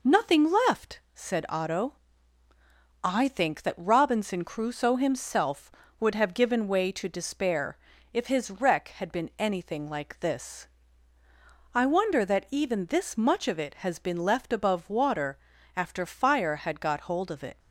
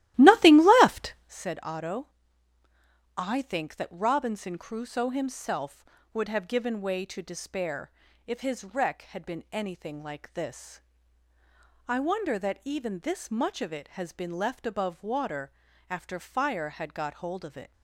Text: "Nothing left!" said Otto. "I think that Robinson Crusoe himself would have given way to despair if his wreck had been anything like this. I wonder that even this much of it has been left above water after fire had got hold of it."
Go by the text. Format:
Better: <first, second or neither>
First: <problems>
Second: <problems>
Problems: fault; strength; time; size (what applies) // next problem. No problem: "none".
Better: first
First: pauses between "despair" and "if"; slight; at 7.7 s; 0.34 s long // pauses between "water" and "after"; at 15.3 s; 0.40 s long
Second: starts louder than the rest; strong; until 1.5 s; 15.5 dB // pauses between "despair" and "if"; slight; at 7.9 s; 0.34 s long // pauses between "water" and "after"; at 15.5 s; 0.40 s long